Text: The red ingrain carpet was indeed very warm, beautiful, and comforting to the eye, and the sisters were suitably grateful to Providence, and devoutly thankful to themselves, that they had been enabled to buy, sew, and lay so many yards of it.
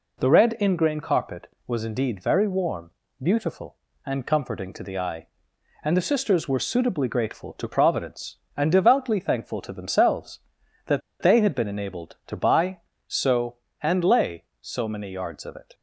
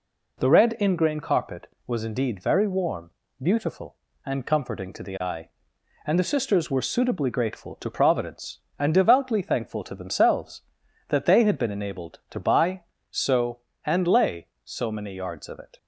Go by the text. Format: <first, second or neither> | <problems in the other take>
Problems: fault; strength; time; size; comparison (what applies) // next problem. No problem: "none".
second | pauses between "that" and "they"; slight; at 11.0 s; 0.21 s long